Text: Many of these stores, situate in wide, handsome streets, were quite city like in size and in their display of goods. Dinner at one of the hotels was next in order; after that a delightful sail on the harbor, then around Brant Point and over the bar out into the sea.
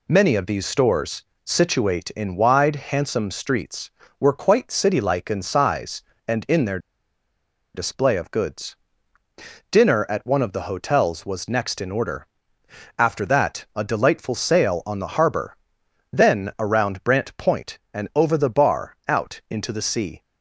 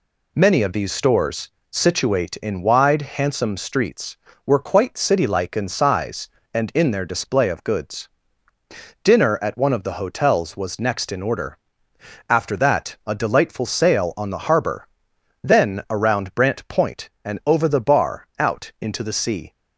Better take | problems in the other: second | pauses between "their" and "display"; noticeable; at 6.7 s; 0.96 s long

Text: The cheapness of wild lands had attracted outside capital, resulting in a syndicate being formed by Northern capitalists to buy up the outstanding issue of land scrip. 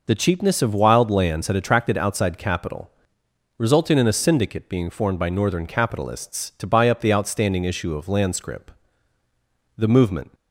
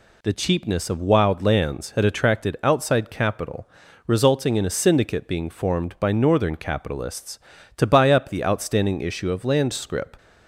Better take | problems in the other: second | goes on to say "The movement"; from 9.7 s on; 0.56 s long

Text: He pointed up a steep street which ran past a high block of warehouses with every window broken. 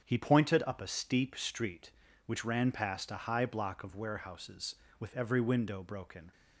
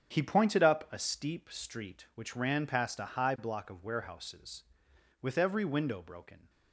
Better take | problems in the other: neither | starts louder than the rest; strong; the same in both

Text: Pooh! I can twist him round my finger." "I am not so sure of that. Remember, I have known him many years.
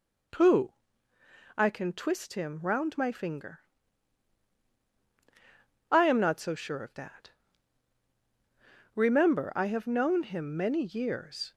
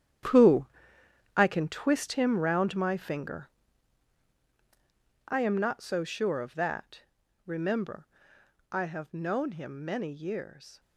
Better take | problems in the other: first | gets quieter; strong; throughout; 13.5 dB

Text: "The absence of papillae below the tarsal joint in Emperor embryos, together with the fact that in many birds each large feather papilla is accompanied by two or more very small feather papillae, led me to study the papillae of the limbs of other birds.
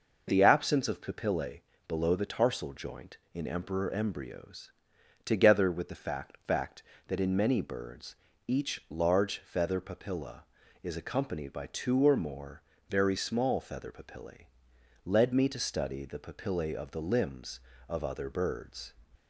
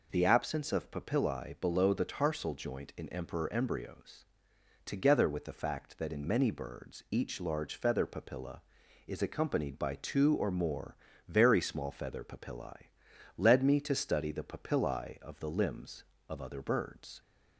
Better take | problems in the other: second | pauses between "papillae" and "below"; slight; at 1.6 s; 0.24 s long // says "fact" twice; at 6.3 s // pauses between "birds" and "each"; slight; at 8.1 s; 0.32 s long // pauses between "more" and "very"; slight; at 12.6 s; 0.30 s long; slight in the second

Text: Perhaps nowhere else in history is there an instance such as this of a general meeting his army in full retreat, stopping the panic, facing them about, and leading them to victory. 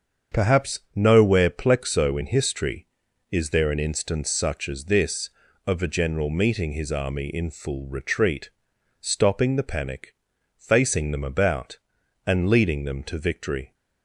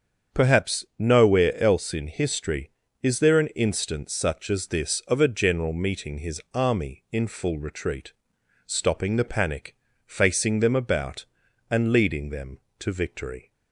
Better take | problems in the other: second | starts louder than the rest; until 1.4 s; 7 dB; strong in the second // pauses between "Perhaps" and "nowhere"; slight; at 0.7 s; 0.16 s long // says "plexo" for "else"; at 1.5 s

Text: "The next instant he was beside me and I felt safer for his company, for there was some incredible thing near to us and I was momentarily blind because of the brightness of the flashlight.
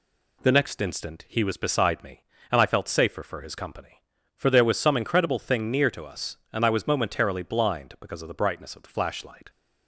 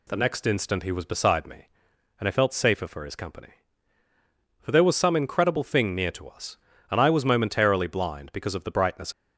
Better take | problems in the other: first | stops before "of the flashlight"; at 9.1 s

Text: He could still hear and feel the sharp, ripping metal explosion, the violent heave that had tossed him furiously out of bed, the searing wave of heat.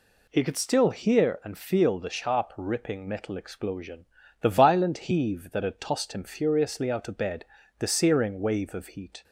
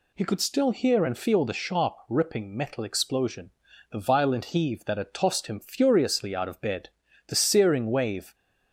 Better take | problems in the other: first | stops before "of heat"; at 8.3 s

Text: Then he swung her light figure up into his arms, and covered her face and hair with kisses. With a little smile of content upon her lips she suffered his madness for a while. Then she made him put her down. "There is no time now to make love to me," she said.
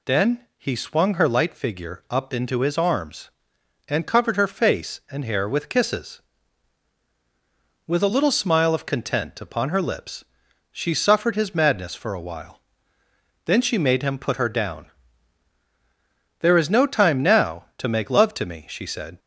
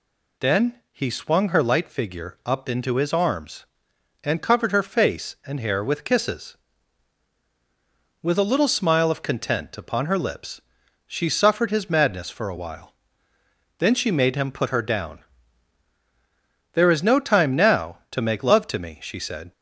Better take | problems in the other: neither | pauses between "Then" and "he"; slight; the same in both // pauses between "lips" and "she"; the same in both

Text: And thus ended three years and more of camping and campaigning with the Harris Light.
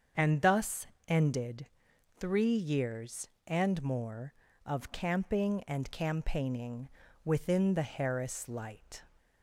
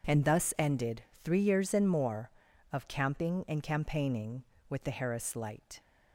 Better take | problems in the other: second | starts louder than the rest; strong; until 1.3 s; 7 dB // pauses between "thus" and "ended"; slight; at 0.8 s; 0.20 s long // pauses between "ended" and "three"; noticeable; at 1.6 s; 0.52 s long; slight in the second // says "within" for "with"; at 7.2 s

